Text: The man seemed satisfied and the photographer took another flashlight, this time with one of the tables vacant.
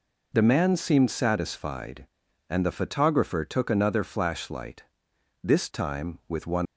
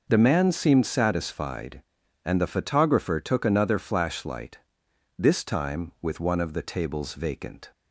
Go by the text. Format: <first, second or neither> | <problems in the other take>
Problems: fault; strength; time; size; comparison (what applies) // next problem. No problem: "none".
second | stops before "of the tables vacant"; at 6.6 s